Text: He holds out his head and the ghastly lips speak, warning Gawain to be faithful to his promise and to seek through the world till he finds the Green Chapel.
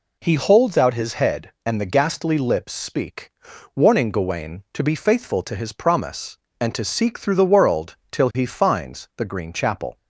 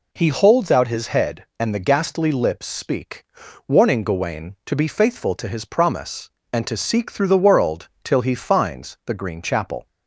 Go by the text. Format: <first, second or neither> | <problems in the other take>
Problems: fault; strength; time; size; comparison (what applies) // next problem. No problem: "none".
neither | none